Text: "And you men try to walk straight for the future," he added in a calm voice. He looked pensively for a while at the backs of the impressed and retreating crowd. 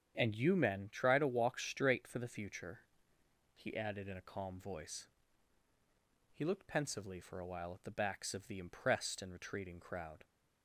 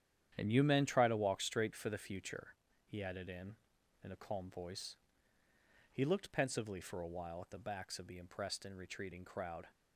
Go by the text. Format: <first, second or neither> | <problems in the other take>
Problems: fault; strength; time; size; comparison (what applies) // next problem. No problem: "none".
first | starts louder than the rest; strong; until 1.3 s; 10 dB; strong in the first // says "in" twice; at 4.0 s